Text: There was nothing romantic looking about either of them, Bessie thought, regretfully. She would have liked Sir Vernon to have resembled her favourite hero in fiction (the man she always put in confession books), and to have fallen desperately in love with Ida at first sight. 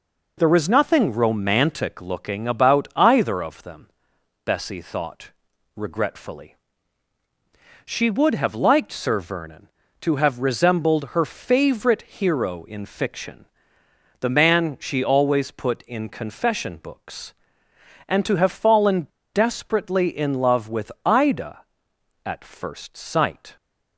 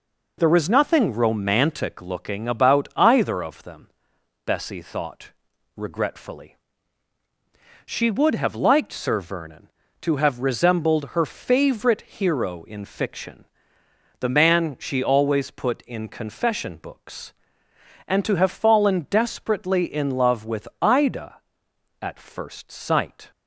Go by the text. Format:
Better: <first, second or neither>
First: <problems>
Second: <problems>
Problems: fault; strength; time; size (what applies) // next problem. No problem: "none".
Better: second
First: pauses between "fallen" and "desperately"; slight; at 19.0 s; 0.25 s long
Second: none